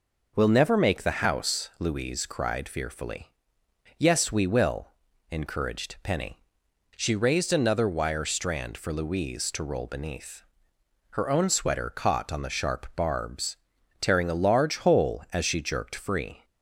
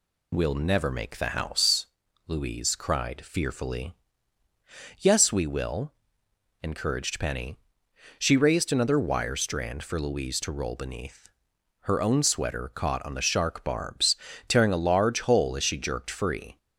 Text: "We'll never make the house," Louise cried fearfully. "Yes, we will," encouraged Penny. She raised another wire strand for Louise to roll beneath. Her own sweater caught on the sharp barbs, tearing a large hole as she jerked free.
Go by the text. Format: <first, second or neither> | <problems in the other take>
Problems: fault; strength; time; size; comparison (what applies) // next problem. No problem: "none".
first | says "shark" for "sharp"; at 13.2 s